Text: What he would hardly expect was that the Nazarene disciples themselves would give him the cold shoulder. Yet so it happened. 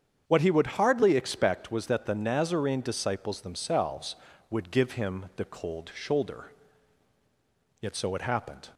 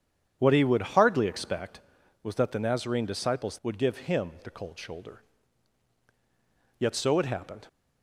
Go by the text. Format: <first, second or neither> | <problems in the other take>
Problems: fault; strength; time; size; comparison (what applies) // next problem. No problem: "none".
first | starts louder than the rest; strong; until 1.4 s; 8.5 dB; strong in the first // skips "themselves"; at 3.6 s